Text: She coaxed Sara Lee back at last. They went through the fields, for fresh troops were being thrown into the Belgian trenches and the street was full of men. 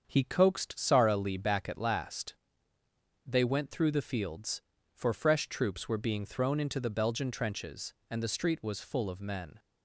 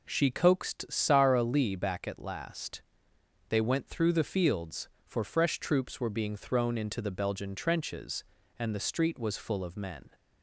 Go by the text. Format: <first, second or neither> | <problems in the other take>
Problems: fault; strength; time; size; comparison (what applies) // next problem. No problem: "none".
second | starts louder than the rest; until 1.0 s; 7 dB // says "He" for "She"; at 0.0 s